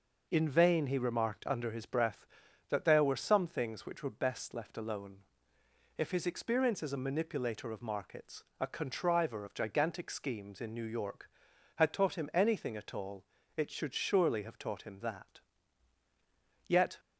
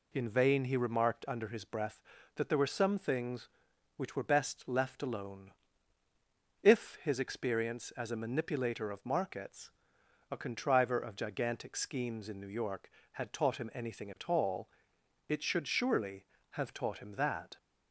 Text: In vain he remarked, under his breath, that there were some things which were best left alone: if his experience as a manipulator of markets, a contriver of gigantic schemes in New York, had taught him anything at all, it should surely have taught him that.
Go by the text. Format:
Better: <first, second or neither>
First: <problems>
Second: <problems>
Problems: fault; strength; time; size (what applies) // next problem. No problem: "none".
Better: second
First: goes on to say "Yet"; slight; from 16.6 s on; 0.30 s long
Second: none